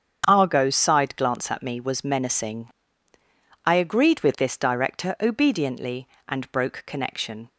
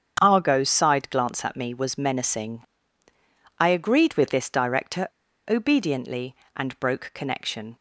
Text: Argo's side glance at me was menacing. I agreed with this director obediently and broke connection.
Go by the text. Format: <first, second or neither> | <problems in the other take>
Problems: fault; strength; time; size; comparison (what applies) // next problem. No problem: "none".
first | starts louder than the rest; strong; until 1.2 s; 7.5 dB; strong in the first // pauses between "director" and "obediently"; at 5.0 s; 0.39 s long